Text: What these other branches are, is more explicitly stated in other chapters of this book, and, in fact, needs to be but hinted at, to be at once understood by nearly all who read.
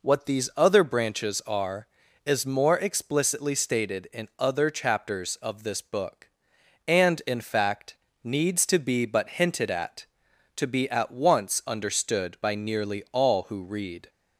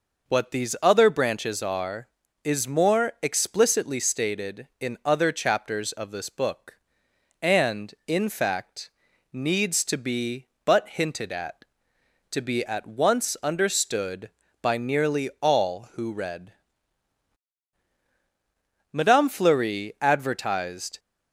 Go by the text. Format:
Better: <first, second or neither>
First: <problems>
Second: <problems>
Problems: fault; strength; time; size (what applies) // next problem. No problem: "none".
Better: first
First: none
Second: goes on to say "Madame Fleury advertised"; strong; from 18.9 s on; 2.0 s long